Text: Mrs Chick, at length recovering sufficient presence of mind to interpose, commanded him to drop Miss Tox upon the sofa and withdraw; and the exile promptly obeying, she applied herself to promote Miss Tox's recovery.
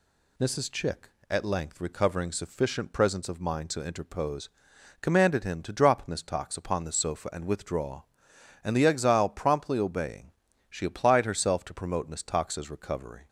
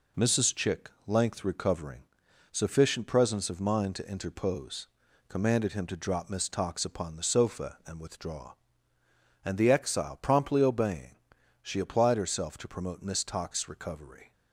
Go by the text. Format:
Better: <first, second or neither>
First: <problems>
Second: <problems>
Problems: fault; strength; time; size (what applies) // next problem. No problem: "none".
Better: first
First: none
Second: skips "at"; at 0.9 s // pauses between "recovering" and "sufficient"; noticeable; at 1.9 s; 0.54 s long